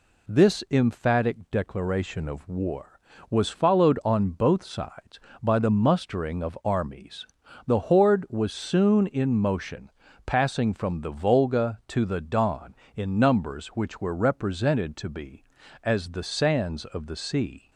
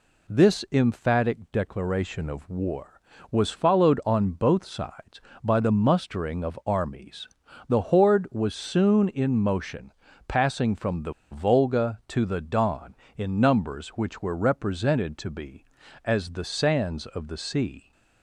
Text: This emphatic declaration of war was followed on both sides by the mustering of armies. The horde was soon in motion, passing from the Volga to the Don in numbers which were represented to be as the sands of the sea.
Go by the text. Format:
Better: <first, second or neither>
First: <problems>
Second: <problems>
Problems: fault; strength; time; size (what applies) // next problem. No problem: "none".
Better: first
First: none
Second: pauses between "the" and "Volga"; slight; at 11.1 s; 0.18 s long